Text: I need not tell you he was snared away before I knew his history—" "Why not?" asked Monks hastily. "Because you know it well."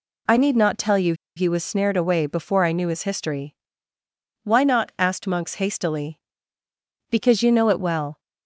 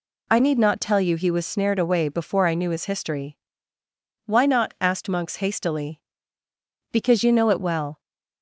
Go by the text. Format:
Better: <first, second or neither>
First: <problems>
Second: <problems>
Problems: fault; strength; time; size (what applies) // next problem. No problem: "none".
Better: second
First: pauses between "you" and "he"; slight; at 1.1 s; 0.23 s long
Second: none